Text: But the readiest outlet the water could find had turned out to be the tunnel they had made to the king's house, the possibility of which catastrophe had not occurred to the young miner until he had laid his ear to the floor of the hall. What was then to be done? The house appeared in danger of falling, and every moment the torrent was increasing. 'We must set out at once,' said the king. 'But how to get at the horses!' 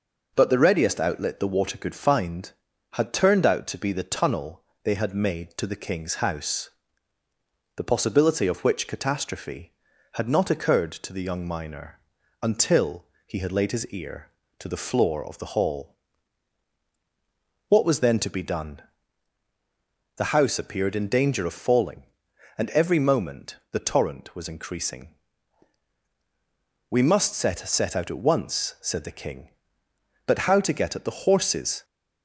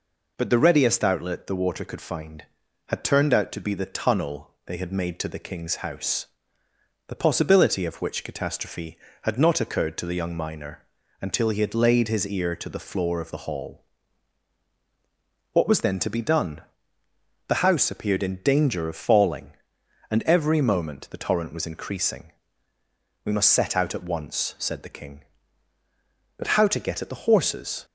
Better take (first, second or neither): second